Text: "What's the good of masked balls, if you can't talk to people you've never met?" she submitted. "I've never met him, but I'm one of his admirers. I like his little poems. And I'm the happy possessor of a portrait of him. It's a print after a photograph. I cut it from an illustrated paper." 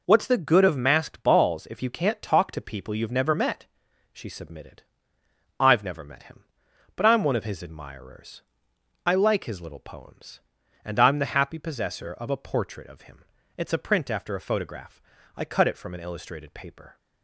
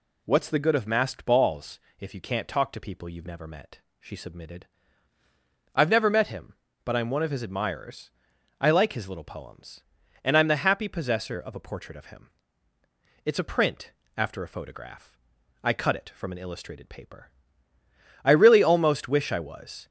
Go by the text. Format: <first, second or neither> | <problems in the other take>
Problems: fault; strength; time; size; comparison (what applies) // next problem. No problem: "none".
first | pauses between "print" and "after"; slight; at 13.9 s; 0.22 s long // goes on to say "I really almost wish I was"; from 18.2 s on; 1.6 s long